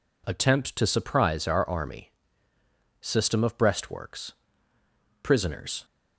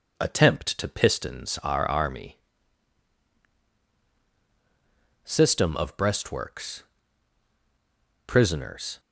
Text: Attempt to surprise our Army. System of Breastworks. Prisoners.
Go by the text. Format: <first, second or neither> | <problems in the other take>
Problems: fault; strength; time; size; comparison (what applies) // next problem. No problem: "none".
first | says "pistons" for "surprise"; at 0.8 s